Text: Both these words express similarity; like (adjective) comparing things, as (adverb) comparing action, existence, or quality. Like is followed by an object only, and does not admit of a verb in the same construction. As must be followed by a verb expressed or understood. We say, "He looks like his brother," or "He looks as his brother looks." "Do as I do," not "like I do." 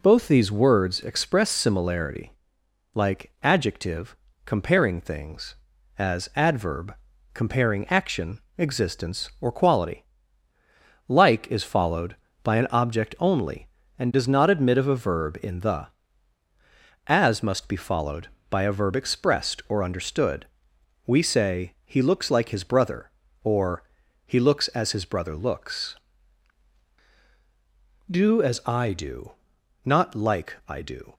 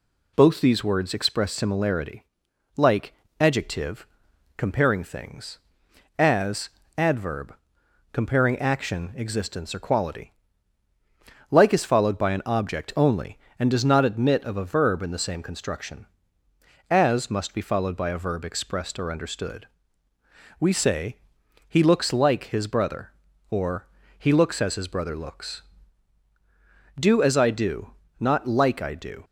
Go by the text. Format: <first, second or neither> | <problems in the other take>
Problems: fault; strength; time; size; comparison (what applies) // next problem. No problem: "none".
second | skips "same construction"; at 16.4 s // pauses between "or" and "He"; at 23.8 s; 0.42 s long; slight in the second